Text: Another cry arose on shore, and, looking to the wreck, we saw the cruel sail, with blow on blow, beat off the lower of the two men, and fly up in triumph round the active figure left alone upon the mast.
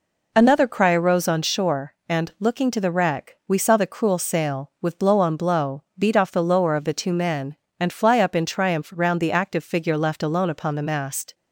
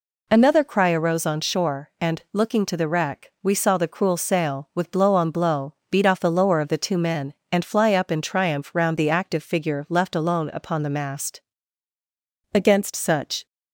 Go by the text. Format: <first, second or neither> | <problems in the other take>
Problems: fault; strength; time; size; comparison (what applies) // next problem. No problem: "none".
first | goes on to say "Against such"; noticeable; from 12.5 s on; 0.92 s long